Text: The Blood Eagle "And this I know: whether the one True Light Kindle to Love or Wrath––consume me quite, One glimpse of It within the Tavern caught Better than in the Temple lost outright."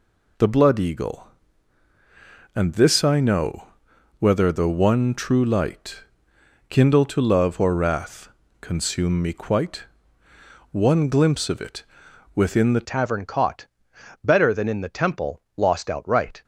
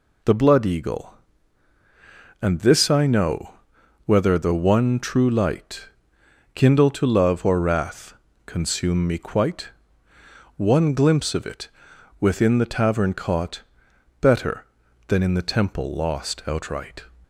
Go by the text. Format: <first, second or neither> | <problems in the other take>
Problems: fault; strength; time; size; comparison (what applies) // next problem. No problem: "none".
second | pauses between "Light" and "Kindle"; noticeable; at 6.0 s; 0.66 s long; noticeable in the second // pauses between "It" and "within"; noticeable; at 11.8 s; 0.50 s long; noticeable in the second // changes voice at "Tavern"; from 12.8 s on; 3.6 s long // pauses between "caught" and "Better"; noticeable; at 13.6 s; 0.60 s long; noticeable in the second